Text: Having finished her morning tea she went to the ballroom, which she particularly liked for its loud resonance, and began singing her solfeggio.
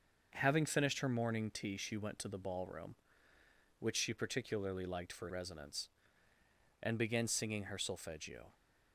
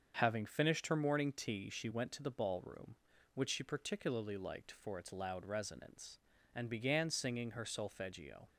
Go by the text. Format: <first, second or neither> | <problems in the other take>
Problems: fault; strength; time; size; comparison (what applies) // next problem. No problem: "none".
second | starts louder than the rest; noticeable; until 1.3 s; 6 dB; also in the second // skips "its loud"; at 5.2 s